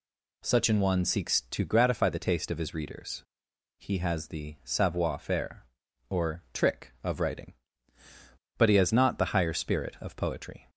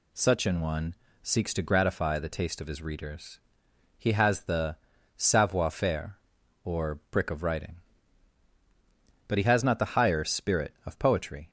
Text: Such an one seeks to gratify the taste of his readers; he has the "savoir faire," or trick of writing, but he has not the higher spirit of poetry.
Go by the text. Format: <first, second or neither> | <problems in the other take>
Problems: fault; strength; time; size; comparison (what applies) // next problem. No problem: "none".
first | pauses between "one" and "seeks"; slight; at 0.9 s; 0.28 s long // pauses between "the" and "savoir"; at 4.7 s; 0.40 s long // says "brick" for "trick"; at 7.1 s